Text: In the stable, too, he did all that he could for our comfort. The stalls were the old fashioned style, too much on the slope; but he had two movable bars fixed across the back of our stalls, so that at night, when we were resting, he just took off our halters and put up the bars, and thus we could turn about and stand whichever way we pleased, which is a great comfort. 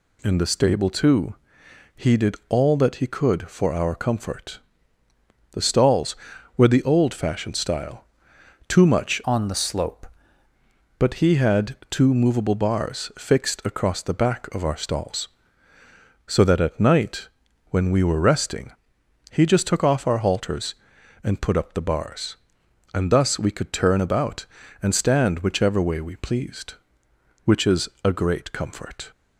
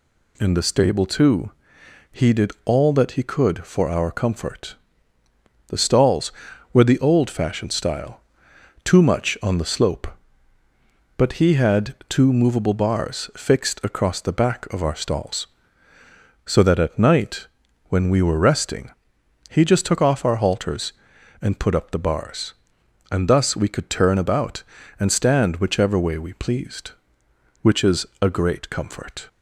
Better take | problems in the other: second | changes voice from "on" to "slope"; from 9.2 to 10.0 s; 0.8 s long // pauses between "is" and "a"; slight; at 27.8 s; 0.16 s long; slight in the second

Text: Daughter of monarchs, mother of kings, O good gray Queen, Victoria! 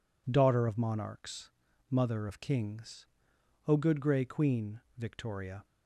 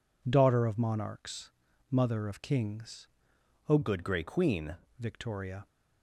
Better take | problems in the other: first | changes voice from "good" to "Queen"; from 3.8 to 4.7 s; 0.9 s long

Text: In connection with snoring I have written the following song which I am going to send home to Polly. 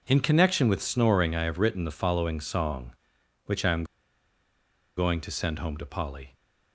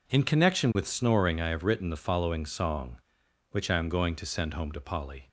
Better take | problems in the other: second | pauses between "am" and "going"; at 3.8 s; 1.1 s long

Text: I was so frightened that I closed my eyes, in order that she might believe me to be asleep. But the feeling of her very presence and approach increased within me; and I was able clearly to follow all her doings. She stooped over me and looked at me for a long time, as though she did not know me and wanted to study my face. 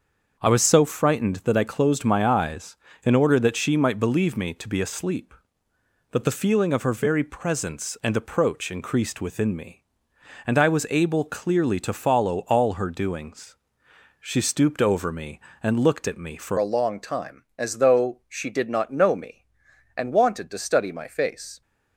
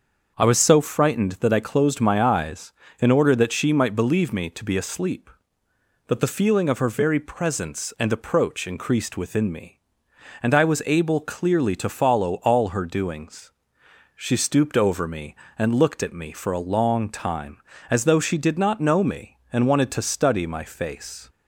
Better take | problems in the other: second | starts louder than the rest; until 1.5 s; 6.5 dB; also in the second // changes voice at "a"; from 16.5 s on; 5.1 s long

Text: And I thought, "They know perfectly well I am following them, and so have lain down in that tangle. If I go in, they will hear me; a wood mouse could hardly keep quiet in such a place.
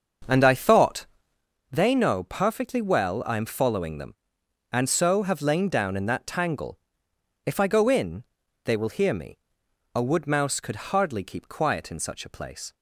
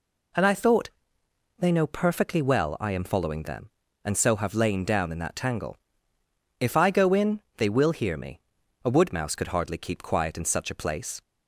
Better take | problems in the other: second | starts louder than the rest; until 1.4 s; 6.5 dB

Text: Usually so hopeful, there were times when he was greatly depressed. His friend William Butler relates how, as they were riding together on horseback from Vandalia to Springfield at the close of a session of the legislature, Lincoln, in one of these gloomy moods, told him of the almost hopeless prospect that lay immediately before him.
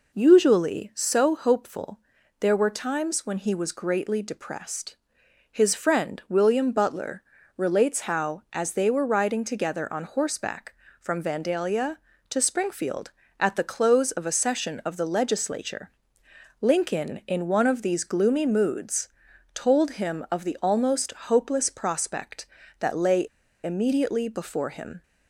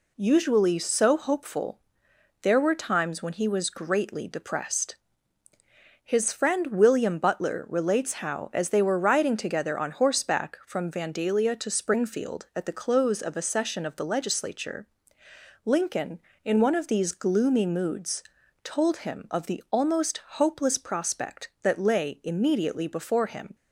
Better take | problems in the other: second | pauses between "Butler" and "relates"; slight; at 7.2 s; 0.34 s long // pauses between "lay" and "immediately"; at 23.2 s; 0.38 s long

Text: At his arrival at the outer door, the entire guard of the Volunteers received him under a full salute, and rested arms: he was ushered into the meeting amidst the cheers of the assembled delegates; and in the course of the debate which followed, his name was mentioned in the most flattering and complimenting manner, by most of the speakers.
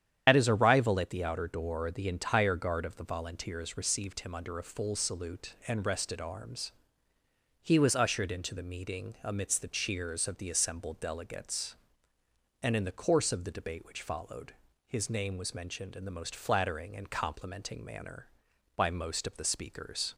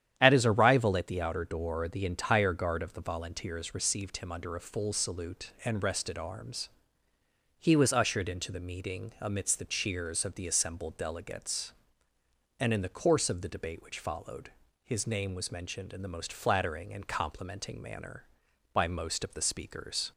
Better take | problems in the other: second | loses the start of "At"; at 0.2 s; 65 ms // starts louder than the rest; strong; until 1.2 s; 9 dB; strong in the second

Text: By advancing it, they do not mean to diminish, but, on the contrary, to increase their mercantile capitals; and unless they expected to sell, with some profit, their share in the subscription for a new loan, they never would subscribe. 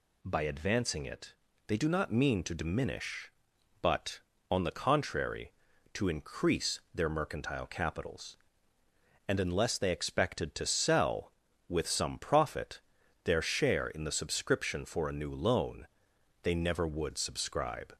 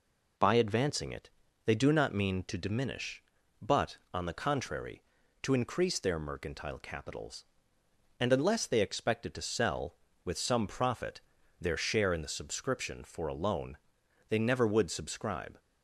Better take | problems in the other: first | skips "new"; at 13.3 s

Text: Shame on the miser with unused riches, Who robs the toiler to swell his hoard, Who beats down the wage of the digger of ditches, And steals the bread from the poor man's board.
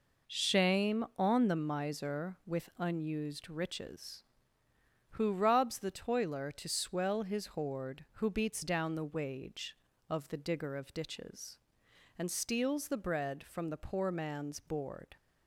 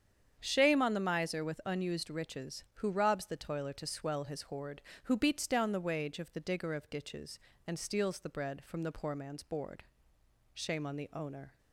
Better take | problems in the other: first | starts louder than the rest; strong; until 1.4 s; 8 dB // goes on to say "Shame on the owner"; noticeable; from 10.5 s on; 1.0 s long

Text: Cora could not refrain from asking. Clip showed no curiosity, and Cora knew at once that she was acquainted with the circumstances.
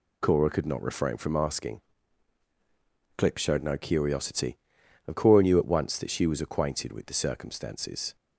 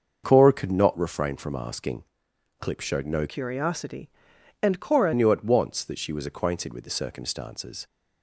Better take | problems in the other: first | starts louder than the rest; until 1.2 s; 6 dB // changes voice from "curiosity" to "Cora"; from 3.2 to 5.1 s; 1.9 s long

